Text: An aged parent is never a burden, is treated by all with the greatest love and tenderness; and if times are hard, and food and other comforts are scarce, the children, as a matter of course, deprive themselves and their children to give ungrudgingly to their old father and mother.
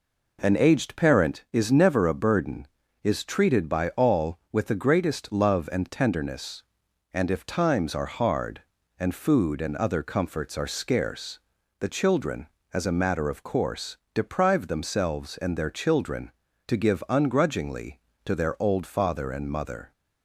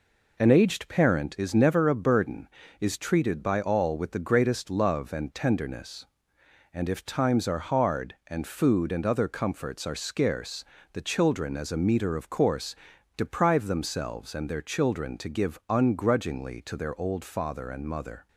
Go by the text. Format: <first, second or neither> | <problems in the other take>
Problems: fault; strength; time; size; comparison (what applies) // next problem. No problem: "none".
first | says "meter" for "matter"; at 11.7 s